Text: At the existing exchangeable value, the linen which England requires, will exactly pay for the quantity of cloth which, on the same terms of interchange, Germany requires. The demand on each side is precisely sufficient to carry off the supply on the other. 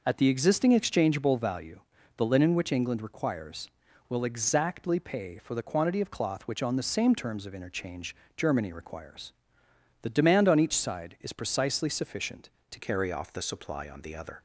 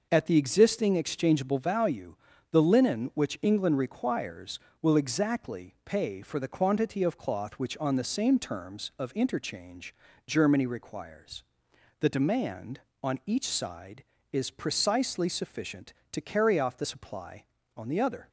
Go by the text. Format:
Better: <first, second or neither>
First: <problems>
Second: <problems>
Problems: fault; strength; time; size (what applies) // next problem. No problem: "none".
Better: second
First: changes voice at "carry"; from 12.7 s on; 1.7 s long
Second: none